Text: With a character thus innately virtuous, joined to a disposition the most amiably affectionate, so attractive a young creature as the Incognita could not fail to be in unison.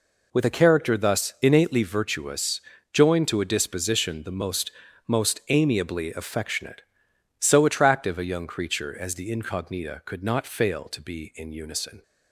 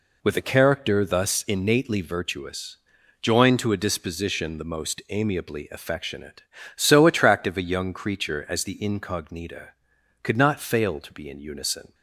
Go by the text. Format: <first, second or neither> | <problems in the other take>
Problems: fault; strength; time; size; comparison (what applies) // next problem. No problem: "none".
second | says "most" twice; at 5.0 s